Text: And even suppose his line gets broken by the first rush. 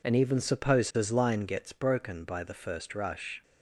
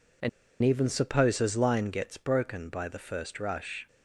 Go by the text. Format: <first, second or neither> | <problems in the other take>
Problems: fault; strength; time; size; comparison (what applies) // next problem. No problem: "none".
first | pauses between "And" and "even"; slight; at 0.2 s; 0.33 s long